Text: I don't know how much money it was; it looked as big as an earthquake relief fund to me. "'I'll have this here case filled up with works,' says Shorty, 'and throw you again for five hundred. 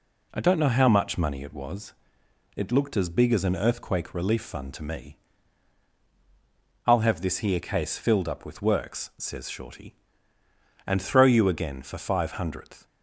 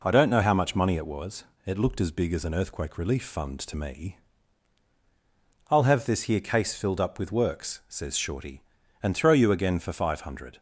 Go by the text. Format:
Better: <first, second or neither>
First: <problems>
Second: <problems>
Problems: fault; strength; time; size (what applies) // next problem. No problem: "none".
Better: second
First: says "hundredth" for "hundred"; at 12.3 s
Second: none